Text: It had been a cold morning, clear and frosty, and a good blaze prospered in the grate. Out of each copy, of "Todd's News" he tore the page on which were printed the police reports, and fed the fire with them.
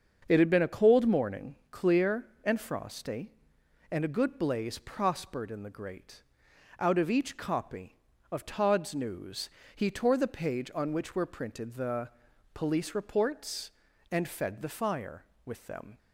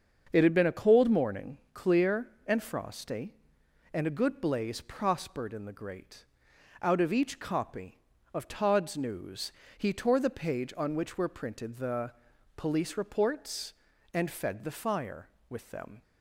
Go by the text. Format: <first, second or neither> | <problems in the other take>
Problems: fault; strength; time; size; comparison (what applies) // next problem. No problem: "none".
neither | starts louder than the rest; the same in both // pauses between "News" and "he"; slight; the same in both // pauses between "the" and "police"; noticeable; the same in both